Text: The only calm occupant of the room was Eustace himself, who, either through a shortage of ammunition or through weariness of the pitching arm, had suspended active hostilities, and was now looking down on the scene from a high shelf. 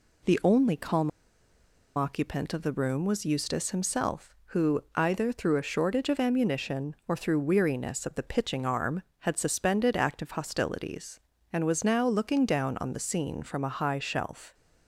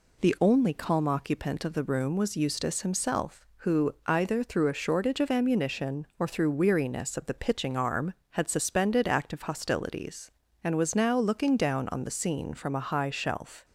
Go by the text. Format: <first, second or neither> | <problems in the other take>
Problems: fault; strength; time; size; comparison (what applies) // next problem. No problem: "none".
second | pauses between "calm" and "occupant"; noticeable; at 1.0 s; 0.86 s long